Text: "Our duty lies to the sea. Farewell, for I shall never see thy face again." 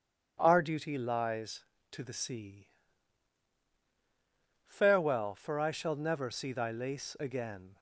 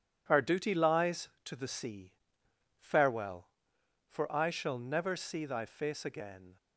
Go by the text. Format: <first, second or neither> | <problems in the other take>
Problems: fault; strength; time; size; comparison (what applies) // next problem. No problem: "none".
second | starts louder than the rest; strong; until 1.3 s; 9 dB // says "lace" for "face"; at 6.7 s